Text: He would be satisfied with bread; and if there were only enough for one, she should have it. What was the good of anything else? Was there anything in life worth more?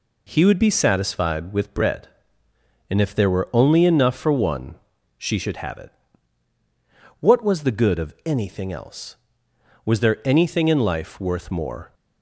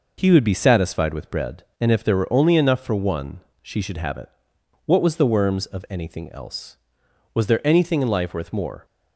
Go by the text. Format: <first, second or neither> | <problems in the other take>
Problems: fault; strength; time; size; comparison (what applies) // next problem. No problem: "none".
first | says "worms" for "good"; at 5.3 s